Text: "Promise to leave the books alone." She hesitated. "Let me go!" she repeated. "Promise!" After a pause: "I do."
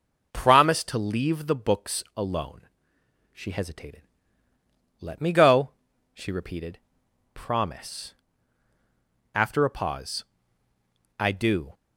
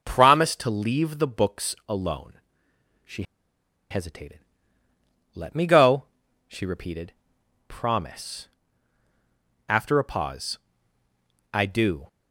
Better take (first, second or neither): first